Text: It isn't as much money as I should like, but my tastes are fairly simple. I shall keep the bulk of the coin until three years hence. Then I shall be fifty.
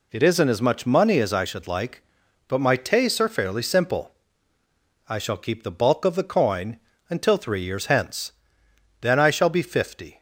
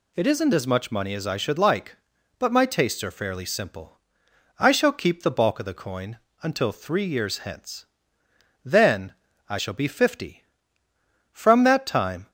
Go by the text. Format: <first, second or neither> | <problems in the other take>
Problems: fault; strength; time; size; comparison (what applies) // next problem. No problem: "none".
first | pauses between "coin" and "until"; slight; at 6.1 s; 0.24 s long; slight in the first // pauses between "Then" and "I"; slight; at 9.1 s; 0.34 s long // goes on to say "From that time"; noticeable; from 11.3 s on; 0.98 s long